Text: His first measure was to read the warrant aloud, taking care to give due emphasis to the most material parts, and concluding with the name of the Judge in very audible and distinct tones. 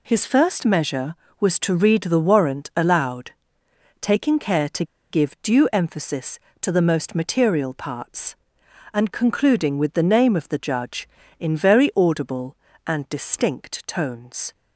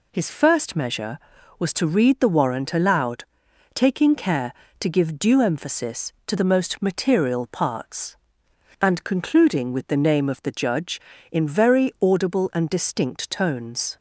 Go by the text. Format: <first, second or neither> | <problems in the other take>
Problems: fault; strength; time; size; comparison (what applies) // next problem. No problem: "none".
second | pauses between "to" and "give"; slight; at 4.8 s; 0.26 s long